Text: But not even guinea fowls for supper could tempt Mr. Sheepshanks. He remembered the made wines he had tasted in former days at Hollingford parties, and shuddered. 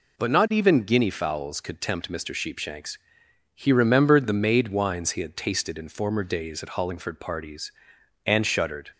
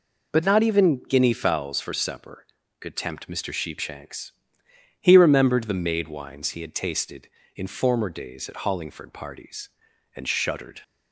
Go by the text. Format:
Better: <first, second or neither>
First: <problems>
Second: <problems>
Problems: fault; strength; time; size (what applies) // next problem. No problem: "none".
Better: second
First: skips "for supper"; at 1.6 s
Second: none